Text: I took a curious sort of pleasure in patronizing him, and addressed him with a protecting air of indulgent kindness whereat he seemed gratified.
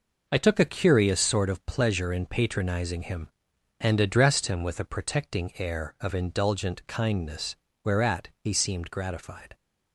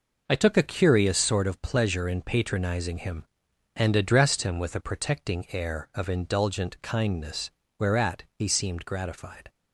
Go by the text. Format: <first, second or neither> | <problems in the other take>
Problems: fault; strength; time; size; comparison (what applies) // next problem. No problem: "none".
neither | pauses between "kindness" and "whereat"; slight; the same in both // pauses between "whereat" and "he"; slight; the same in both